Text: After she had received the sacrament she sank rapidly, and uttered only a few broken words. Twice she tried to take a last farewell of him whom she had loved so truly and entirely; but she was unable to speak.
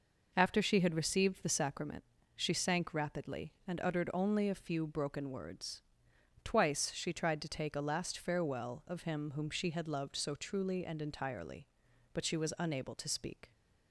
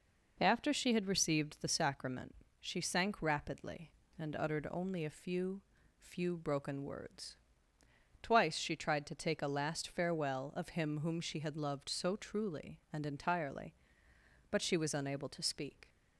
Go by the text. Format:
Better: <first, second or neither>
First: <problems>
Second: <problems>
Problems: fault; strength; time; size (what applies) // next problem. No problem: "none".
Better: first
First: pauses between "sacrament" and "she"; slight; at 2.0 s; 0.34 s long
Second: pauses between "sacrament" and "she"; slight; at 2.3 s; 0.28 s long // says "few" twice; at 5.9 s